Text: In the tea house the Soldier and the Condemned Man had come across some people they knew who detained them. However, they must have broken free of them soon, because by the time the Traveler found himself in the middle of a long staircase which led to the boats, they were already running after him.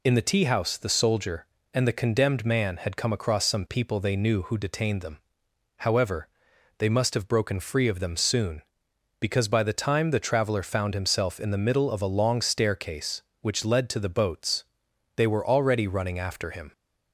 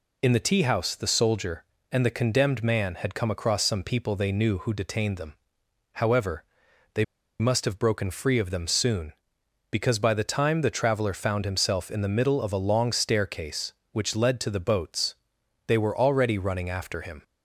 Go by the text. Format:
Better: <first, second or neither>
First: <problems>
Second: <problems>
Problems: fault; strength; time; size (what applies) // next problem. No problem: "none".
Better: first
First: none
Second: pauses between "they" and "must"; slight; at 7.0 s; 0.35 s long